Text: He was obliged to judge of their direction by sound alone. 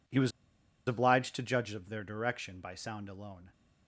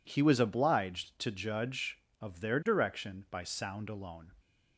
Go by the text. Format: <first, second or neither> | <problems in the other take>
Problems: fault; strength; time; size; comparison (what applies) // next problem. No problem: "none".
second | pauses between "was" and "obliged"; noticeable; at 0.3 s; 0.56 s long